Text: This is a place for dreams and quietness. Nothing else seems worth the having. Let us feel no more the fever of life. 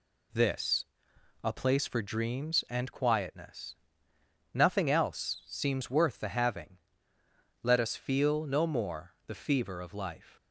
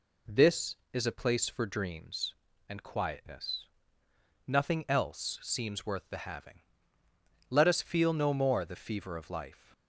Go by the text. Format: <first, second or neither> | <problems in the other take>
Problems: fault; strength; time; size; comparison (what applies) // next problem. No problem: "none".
second | skips "is"; at 1.1 s